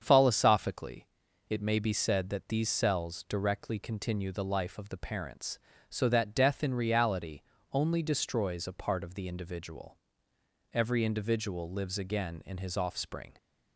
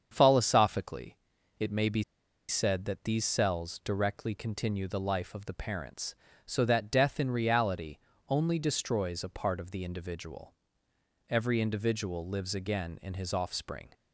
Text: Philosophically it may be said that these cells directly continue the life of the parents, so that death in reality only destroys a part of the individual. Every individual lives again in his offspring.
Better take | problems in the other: first | starts louder than the rest; strong; until 1.1 s; 7.5 dB; strong in the first // pauses between "Philosophically" and "it"; at 1.1 s; 0.42 s long; also in the first // pauses between "be" and "said"; noticeable; at 2.0 s; 0.46 s long // pauses between "reality" and "only"; slight; at 7.9 s; 0.30 s long; slight in the first

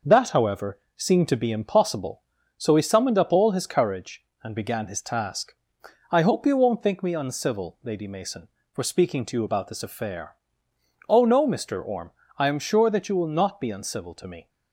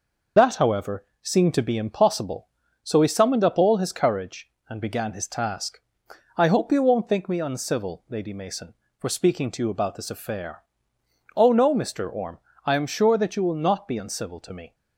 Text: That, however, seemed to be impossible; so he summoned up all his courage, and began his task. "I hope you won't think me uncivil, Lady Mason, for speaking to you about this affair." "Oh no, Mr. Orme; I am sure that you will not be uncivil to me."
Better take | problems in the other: first | loses the start of "That"; at 0.3 s; 55 ms

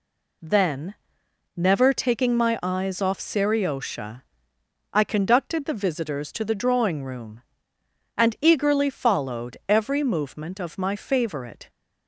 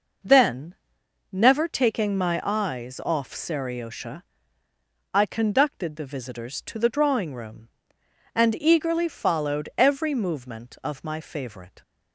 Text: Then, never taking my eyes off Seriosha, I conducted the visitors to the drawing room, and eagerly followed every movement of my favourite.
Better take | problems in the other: neither | none

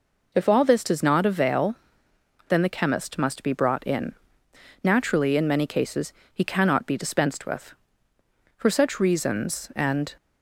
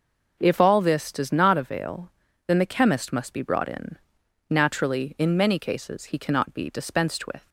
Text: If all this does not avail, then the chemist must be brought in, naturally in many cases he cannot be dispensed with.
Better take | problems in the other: second | pauses between "cases" and "he"; slight; at 6.1 s; 0.20 s long // goes on to say "For such reasons and"; from 8.5 s on; 1.5 s long

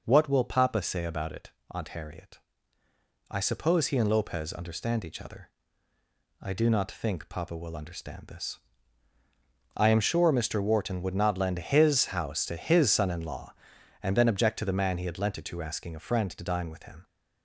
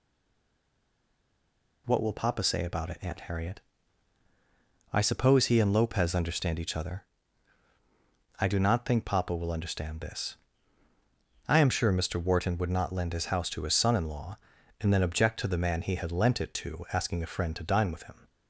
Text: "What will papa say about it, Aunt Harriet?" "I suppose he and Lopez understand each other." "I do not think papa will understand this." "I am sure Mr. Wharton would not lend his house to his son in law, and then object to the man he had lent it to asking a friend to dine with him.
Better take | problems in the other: first | stays silent before the first word; noticeable; until 1.8 s; 1.8 s long

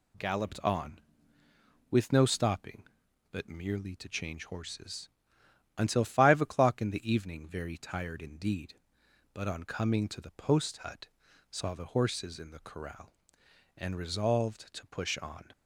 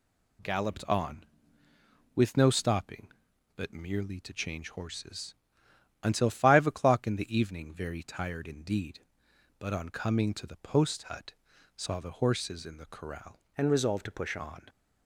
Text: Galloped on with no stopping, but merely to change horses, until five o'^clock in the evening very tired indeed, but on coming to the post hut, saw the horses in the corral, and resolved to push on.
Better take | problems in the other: first | changes voice from "and" to "push"; from 13.5 to 14.3 s; 0.8 s long

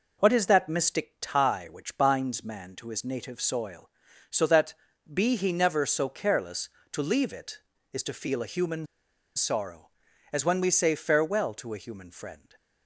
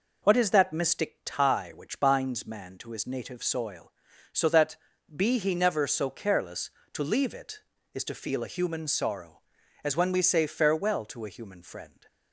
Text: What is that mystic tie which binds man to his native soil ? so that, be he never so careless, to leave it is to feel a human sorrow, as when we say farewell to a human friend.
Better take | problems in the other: second | pauses between "human" and "sorrow"; noticeable; at 8.8 s; 0.50 s long

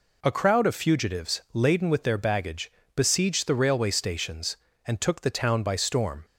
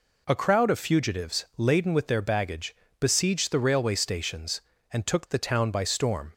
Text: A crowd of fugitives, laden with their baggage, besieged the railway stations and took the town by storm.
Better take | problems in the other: neither | none

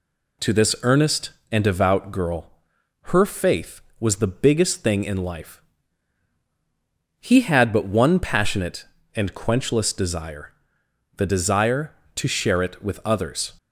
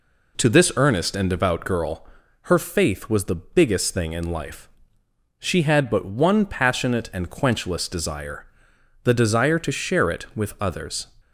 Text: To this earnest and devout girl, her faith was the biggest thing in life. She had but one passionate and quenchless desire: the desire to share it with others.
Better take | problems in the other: second | says "He" for "She"; at 7.1 s

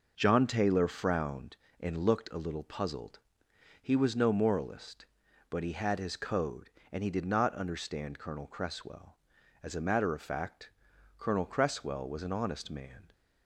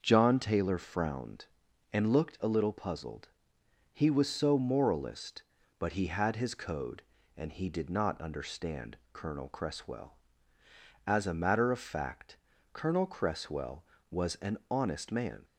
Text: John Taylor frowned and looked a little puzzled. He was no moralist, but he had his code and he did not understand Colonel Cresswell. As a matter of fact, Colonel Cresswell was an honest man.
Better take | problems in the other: first | starts louder than the rest; until 1.0 s; 6.5 dB // says "so" for "no"; at 4.3 s // pauses between "understand" and "Colonel"; slight; at 8.9 s; 0.16 s long

